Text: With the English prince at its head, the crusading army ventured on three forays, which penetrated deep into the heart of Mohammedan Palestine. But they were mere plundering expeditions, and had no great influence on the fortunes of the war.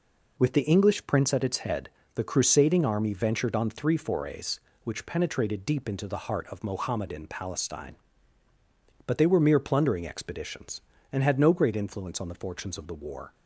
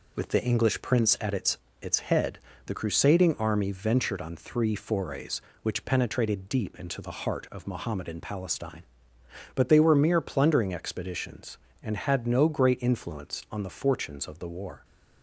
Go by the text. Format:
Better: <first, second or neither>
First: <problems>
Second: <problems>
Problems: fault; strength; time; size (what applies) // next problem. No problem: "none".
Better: first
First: none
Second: says "its" twice; at 1.7 s